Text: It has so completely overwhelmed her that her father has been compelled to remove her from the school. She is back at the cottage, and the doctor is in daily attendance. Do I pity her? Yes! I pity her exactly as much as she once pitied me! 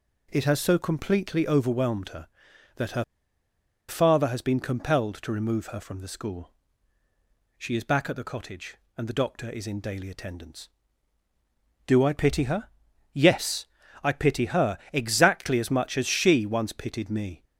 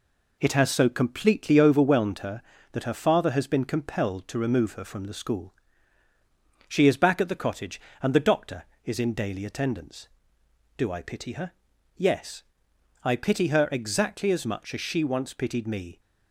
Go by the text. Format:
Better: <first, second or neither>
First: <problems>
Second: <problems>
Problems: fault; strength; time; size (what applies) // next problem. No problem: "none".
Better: second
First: pauses between "her" and "father"; noticeable; at 3.0 s; 0.85 s long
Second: none